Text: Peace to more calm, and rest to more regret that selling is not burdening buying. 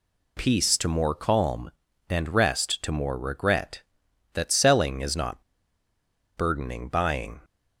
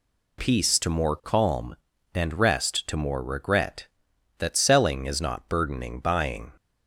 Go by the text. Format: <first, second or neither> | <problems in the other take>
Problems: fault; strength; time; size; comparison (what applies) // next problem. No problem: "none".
second | pauses between "not" and "burdening"; noticeable; at 5.4 s; 0.94 s long